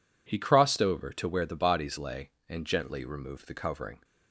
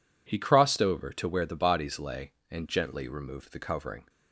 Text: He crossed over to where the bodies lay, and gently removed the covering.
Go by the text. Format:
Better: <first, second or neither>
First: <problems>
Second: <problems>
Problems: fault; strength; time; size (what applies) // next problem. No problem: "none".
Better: neither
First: none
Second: none